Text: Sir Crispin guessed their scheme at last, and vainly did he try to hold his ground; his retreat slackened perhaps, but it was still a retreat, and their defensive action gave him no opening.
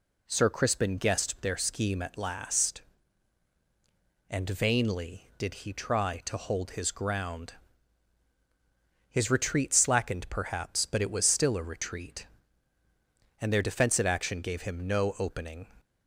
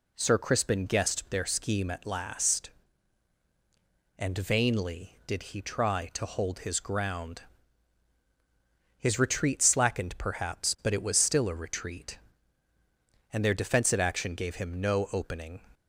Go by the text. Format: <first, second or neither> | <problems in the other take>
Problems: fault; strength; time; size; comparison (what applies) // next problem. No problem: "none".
neither | none